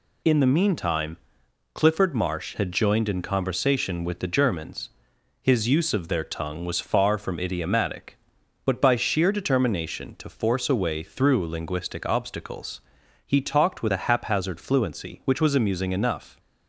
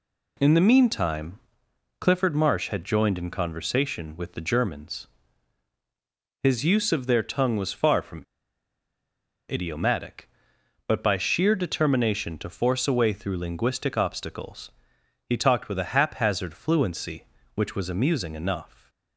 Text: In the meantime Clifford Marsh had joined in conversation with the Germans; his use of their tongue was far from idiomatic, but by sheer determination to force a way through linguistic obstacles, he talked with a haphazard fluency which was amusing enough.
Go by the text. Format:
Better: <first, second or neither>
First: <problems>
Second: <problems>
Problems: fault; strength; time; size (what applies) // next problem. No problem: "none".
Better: first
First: pauses between "meantime" and "Clifford"; noticeable; at 1.1 s; 0.58 s long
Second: pauses between "meantime" and "Clifford"; noticeable; at 1.3 s; 0.58 s long // pauses between "from" and "idiomatic"; strong; at 8.2 s; 1.2 s long